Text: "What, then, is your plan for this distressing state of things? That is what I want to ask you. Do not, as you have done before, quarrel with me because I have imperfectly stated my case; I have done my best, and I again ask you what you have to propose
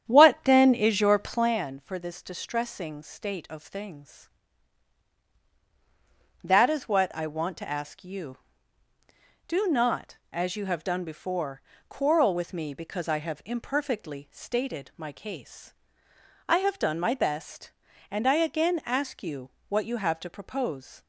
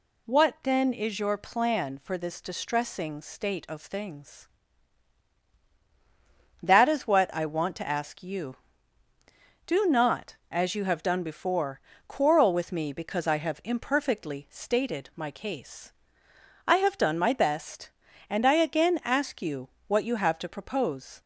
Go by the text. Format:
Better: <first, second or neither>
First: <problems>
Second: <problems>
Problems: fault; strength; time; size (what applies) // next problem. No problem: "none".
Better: second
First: starts louder than the rest; strong; until 1.6 s; 9.5 dB // pauses between "you" and "what"; slight; at 19.5 s; 0.18 s long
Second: pauses between "you" and "what"; slight; at 19.7 s; 0.18 s long